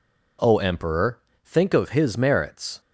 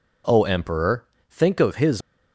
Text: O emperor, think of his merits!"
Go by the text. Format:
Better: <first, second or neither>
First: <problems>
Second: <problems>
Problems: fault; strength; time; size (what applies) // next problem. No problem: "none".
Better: first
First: none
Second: stops before "merits"; at 2.0 s